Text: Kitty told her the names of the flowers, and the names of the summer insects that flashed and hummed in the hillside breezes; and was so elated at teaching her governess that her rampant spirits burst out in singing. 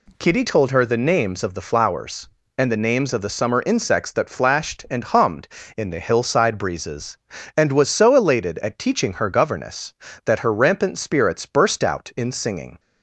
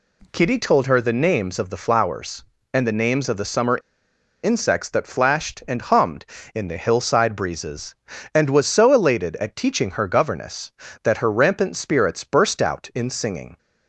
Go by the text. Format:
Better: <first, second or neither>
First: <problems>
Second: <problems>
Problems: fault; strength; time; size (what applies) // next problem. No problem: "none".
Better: first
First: none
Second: pauses between "summer" and "insects"; noticeable; at 3.7 s; 0.65 s long